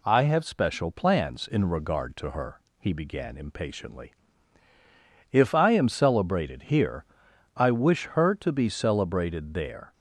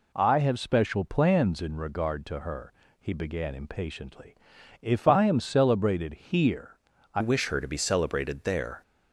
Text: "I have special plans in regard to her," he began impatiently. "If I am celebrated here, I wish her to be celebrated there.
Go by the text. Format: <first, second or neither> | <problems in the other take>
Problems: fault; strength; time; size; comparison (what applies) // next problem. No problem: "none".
first | changes voice at "wish"; from 7.1 s on; 1.7 s long